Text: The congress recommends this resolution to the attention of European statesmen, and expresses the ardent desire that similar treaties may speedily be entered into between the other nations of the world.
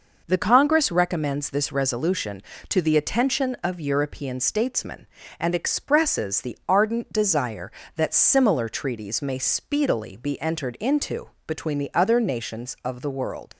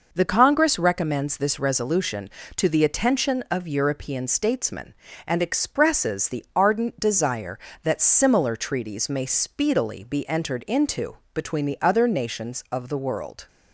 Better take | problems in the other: second | pauses between "into" and "between"; slight; at 11.2 s; 0.18 s long; slight in the second // leaves "world" unfinished; at 13.5 s; 75 ms

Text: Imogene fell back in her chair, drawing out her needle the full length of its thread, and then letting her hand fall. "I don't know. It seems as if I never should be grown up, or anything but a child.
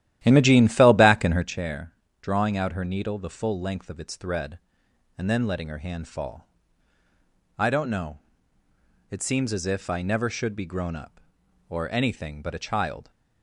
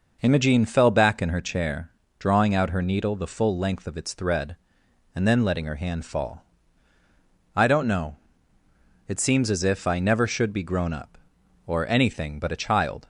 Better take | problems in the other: second | starts louder than the rest; strong; until 1.5 s; 13 dB

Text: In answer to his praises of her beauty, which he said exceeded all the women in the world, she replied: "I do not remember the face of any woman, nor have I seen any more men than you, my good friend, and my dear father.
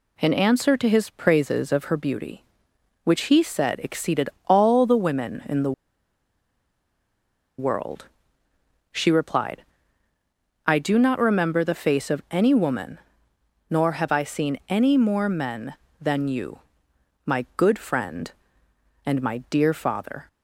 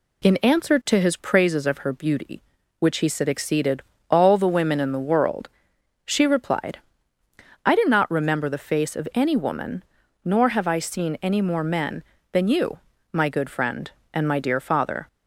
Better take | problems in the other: second | pauses between "exceeded" and "all"; slight; at 4.2 s; 0.18 s long; slight in the second // pauses between "the" and "world"; strong; at 5.7 s; 1.8 s long

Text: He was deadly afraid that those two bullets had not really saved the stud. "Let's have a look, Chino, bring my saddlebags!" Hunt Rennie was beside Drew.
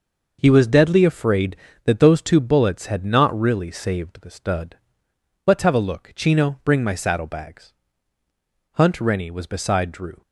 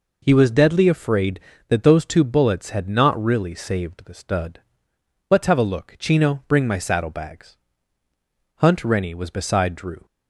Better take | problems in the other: second | gets quieter; strong; throughout; 8 dB

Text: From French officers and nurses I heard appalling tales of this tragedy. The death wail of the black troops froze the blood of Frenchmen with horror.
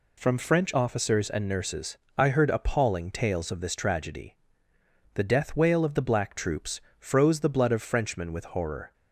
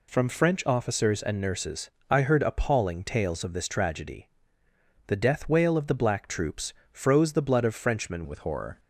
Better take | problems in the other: first | pauses between "nurses" and "I"; slight; at 1.9 s; 0.18 s long; slight in the first // pauses between "troops" and "froze"; slight; at 6.7 s; 0.18 s long; slight in the first // changes voice at "with"; from 8.2 s on; 0.5 s long

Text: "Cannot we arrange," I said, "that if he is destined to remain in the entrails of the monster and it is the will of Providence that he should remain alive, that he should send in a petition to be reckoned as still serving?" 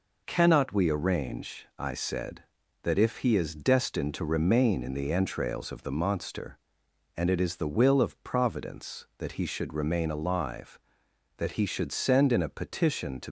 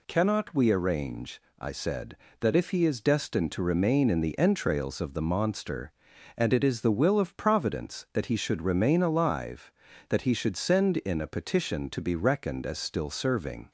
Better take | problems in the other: second | stops before "be reckoned as still serving"; at 13.2 s

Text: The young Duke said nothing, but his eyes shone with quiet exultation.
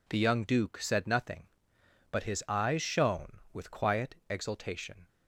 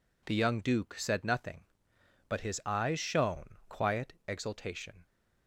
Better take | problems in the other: first | skips "with"; at 3.6 s // pauses between "quiet" and "exultation"; slight; at 4.1 s; 0.16 s long; slight in the first

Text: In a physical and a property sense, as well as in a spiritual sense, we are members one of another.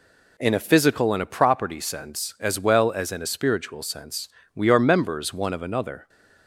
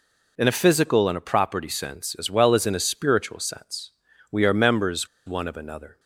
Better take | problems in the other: first | pauses between "members" and "one"; slight; at 5.0 s; 0.18 s long

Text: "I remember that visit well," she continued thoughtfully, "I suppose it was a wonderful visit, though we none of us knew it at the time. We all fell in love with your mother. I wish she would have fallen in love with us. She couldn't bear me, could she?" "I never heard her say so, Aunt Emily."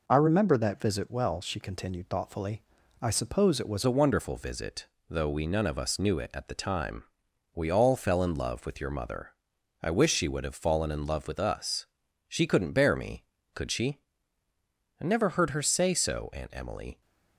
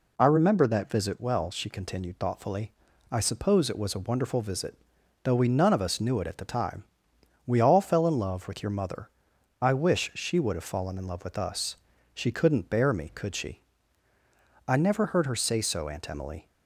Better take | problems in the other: second | changes voice at "a"; from 3.8 s on; 13.2 s long

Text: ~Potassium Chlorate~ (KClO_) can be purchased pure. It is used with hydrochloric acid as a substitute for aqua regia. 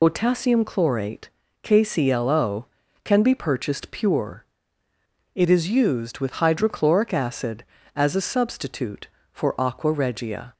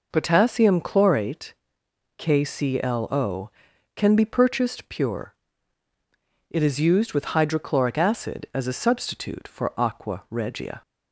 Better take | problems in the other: second | loses the start of "Potassium"; at 0.0 s; 60 ms

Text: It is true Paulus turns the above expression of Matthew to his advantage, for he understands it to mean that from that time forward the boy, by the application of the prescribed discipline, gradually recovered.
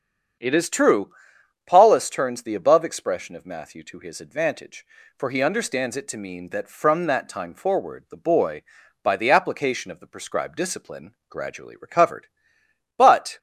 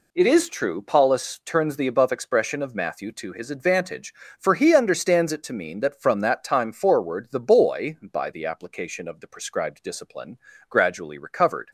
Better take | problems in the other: second | starts louder than the rest; strong; until 1.9 s; 7.5 dB // pauses between "true" and "Paulus"; noticeable; at 1.0 s; 0.56 s long // goes on to say "But"; slight; from 12.9 s on; 0.40 s long

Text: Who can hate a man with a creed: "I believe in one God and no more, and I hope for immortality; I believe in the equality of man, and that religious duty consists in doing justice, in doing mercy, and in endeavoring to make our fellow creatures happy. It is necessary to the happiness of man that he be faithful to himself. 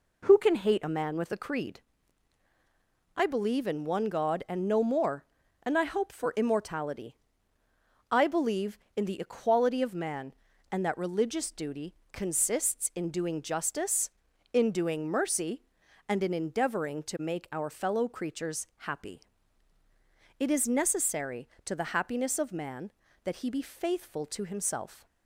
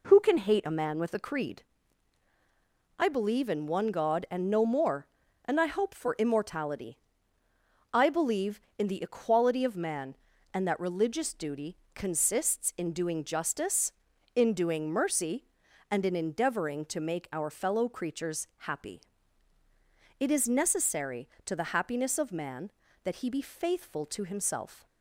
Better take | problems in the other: neither | pauses between "duty" and "consists"; slight; the same in both

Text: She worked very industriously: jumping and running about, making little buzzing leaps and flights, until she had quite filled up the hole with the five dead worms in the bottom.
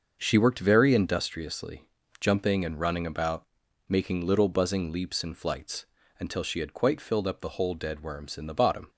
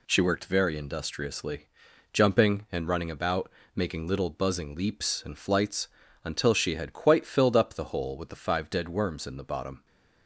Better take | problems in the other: second | starts louder than the rest; until 1.2 s; 6.5 dB // skips "with the five"; at 7.7 s

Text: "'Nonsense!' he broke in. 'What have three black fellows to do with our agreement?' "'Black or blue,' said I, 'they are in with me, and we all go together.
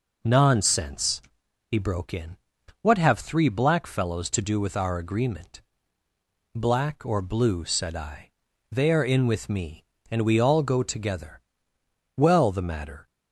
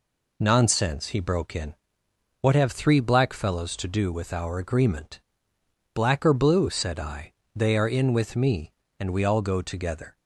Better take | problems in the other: second | goes on to say "Well the matter"; noticeable; from 12.1 s on; 0.92 s long

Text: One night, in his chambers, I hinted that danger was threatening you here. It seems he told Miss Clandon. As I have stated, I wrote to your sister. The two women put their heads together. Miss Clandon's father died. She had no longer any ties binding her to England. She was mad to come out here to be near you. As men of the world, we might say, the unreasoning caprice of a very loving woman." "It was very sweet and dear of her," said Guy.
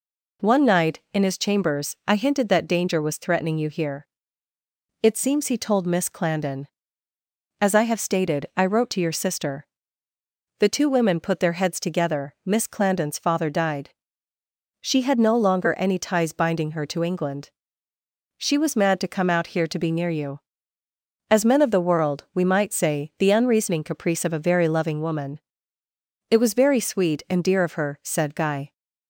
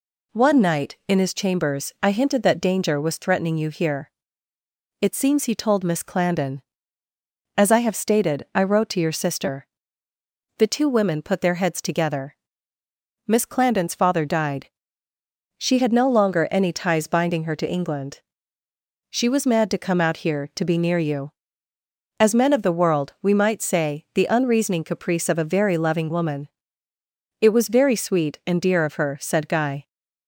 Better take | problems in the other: neither | none

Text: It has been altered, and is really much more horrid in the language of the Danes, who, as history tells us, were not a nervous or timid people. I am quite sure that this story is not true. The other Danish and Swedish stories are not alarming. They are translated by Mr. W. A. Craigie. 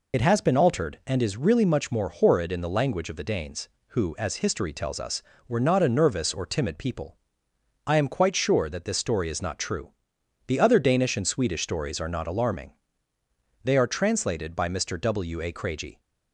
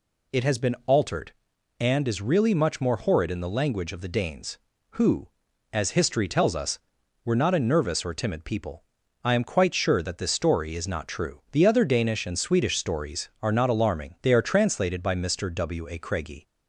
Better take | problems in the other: second | loses the start of "It"; at 0.1 s; 45 ms

